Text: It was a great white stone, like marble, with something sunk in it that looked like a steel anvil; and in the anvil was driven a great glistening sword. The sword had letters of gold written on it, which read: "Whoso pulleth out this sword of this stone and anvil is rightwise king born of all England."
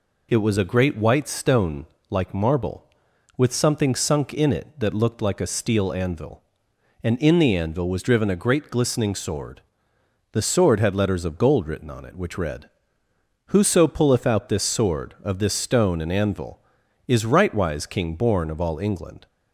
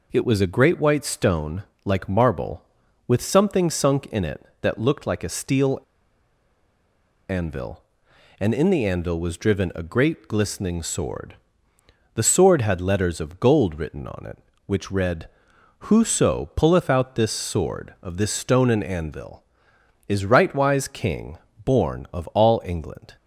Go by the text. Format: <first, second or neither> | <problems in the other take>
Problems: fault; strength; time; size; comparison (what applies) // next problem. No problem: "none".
first | pauses between "steel" and "anvil"; strong; at 5.7 s; 1.5 s long // pauses between "king" and "born"; slight; at 21.3 s; 0.26 s long